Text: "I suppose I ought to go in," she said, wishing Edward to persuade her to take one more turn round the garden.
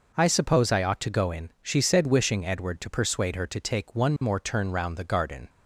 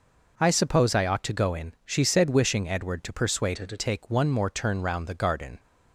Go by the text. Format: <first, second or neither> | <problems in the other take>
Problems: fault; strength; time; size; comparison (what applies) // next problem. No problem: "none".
first | changes voice from "her" to "to"; from 3.5 to 3.7 s; 0.2 s long